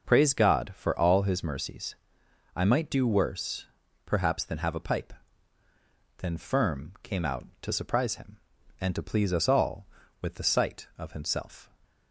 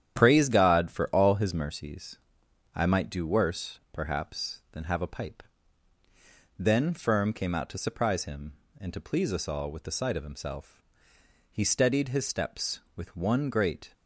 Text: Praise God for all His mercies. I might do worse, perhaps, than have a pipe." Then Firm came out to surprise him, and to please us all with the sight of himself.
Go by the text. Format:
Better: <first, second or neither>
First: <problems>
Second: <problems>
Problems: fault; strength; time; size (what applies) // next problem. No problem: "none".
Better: first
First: none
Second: starts louder than the rest; strong; until 1.2 s; 10 dB // goes on to say "He steadied his steps with one great"; strong; from 11.5 s on; 2.4 s long